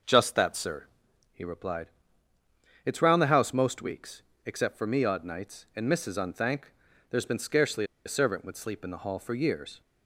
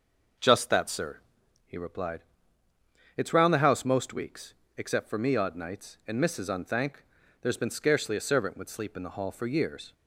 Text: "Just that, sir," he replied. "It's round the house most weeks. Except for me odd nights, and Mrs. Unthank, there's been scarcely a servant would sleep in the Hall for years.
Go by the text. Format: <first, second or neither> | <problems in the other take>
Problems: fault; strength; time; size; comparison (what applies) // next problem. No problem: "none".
second | starts louder than the rest; noticeable; until 1.5 s; 6 dB; noticeable in the second // pauses between "scarcely" and "a"; slight; at 7.8 s; 0.20 s long